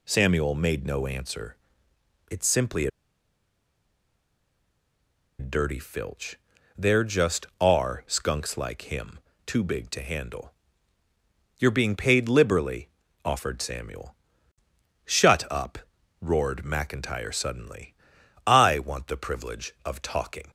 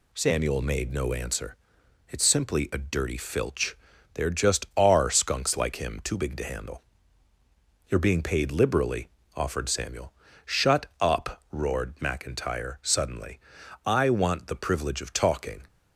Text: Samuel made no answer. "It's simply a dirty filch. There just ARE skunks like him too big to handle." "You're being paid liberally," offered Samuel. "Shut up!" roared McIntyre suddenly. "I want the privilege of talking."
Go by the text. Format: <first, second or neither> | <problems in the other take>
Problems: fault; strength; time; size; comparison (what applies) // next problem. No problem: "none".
second | pauses between "simply" and "a"; strong; at 2.8 s; 2.5 s long // pauses between "him" and "too"; slight; at 9.2 s; 0.26 s long